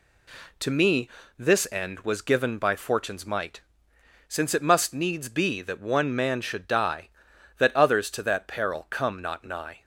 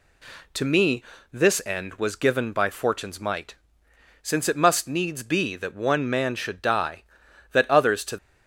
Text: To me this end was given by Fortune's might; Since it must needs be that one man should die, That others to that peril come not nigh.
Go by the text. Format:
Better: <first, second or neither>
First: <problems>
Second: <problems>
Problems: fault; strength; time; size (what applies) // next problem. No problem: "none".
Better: first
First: pauses between "me" and "this"; slight; at 1.0 s; 0.30 s long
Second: pauses between "me" and "this"; slight; at 1.0 s; 0.30 s long // stops before "that peril come not nigh"; at 8.1 s